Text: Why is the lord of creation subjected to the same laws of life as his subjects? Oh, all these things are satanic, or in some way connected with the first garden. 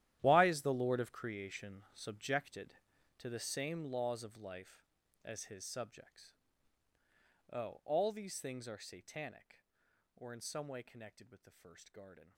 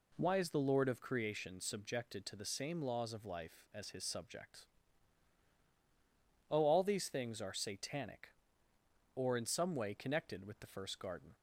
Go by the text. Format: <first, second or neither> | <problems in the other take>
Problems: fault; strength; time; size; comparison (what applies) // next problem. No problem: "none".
second | gets quieter; strong; throughout; 16.5 dB